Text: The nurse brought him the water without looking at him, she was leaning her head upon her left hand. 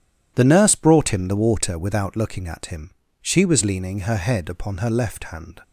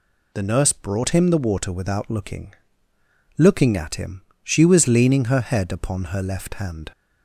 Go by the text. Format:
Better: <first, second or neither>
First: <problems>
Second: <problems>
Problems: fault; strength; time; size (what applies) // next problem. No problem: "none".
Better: first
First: none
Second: says "looking" twice; at 3.4 s